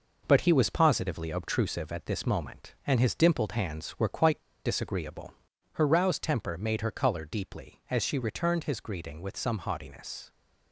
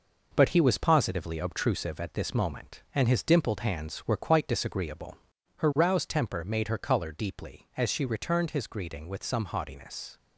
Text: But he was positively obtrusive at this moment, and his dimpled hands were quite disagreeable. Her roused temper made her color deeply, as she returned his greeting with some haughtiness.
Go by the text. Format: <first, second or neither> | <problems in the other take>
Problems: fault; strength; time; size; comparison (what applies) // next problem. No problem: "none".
second | pauses between "quite" and "disagreeable"; slight; at 4.3 s; 0.26 s long